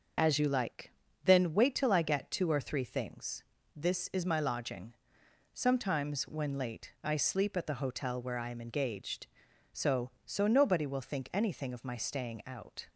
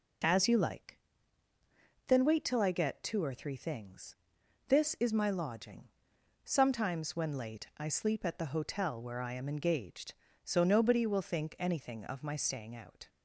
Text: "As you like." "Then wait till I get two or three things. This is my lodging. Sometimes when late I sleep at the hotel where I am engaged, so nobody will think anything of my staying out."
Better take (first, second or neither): second